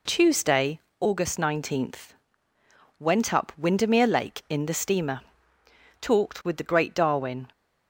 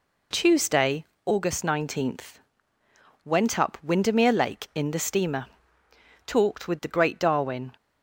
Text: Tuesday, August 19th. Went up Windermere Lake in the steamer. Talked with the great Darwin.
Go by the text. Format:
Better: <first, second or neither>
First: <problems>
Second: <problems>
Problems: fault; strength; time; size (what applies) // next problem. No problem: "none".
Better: neither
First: none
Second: none